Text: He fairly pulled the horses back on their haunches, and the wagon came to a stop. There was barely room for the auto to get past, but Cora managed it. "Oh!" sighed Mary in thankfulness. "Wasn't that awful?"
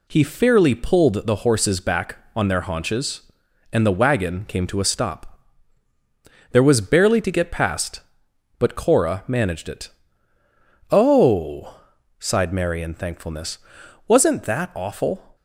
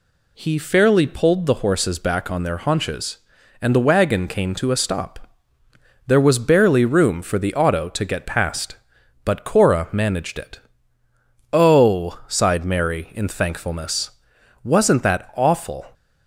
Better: second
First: skips "room for the auto"; at 7.2 s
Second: none

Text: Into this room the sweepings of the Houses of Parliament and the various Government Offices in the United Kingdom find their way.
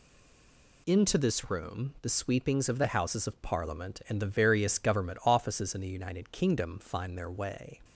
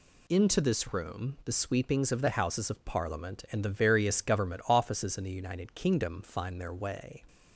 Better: second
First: stays silent before the first word; slight; until 0.8 s; 0.8 s long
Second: none

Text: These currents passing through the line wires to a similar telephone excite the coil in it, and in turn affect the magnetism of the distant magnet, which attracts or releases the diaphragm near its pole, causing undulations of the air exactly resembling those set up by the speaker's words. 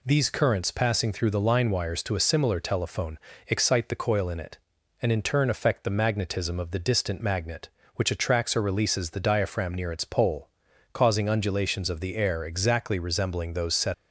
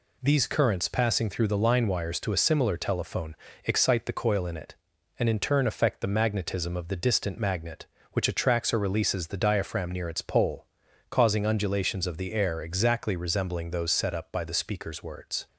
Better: second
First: pauses between "telephone" and "excite"; slight; at 3.1 s; 0.26 s long // stops before "up by the speaker's words"; at 13.9 s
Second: pauses between "telephone" and "excite"; slight; at 3.3 s; 0.26 s long

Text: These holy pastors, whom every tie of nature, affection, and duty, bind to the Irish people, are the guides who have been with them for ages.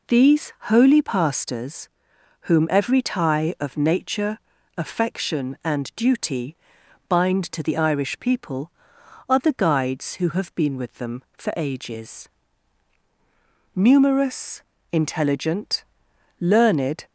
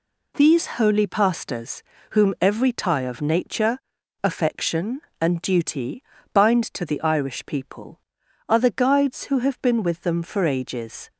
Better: second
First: goes on to say "Numerous intelligent learned"; strong; from 13.7 s on; 3.3 s long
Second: none

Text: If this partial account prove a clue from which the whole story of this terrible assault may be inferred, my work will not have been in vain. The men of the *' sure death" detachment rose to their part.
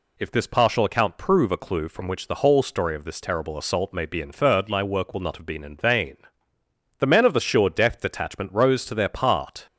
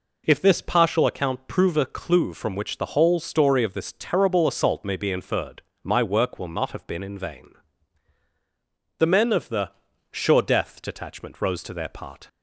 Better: neither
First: none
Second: none

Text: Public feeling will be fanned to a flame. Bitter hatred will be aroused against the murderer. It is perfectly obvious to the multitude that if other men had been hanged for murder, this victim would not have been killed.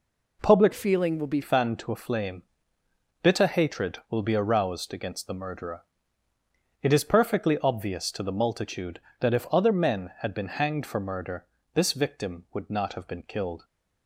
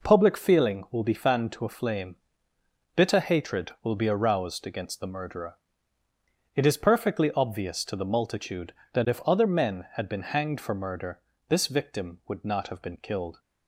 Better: second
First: changes voice from "feeling" to "be"; from 0.7 to 1.4 s; 0.7 s long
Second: none

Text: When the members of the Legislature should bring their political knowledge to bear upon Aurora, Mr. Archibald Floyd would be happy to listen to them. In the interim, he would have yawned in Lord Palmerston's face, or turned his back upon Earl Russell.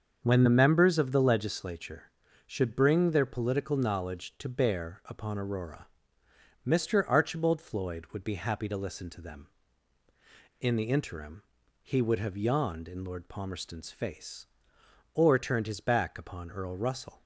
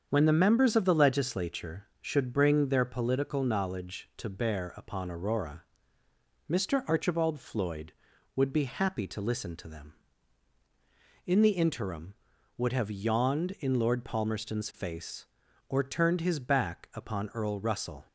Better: first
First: starts louder than the rest; until 1.2 s; 7 dB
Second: starts louder than the rest; strong; until 1.1 s; 7 dB // skips "he"; at 12.3 s

